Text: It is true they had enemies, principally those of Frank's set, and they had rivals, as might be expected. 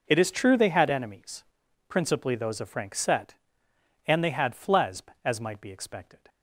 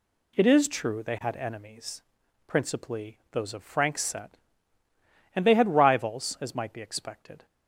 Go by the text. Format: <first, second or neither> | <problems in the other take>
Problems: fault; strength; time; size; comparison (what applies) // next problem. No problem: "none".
second | says "flesb" for "rivals"; at 4.5 s